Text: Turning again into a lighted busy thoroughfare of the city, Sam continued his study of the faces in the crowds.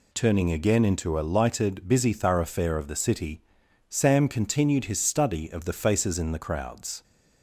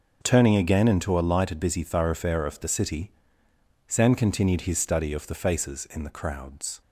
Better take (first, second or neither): neither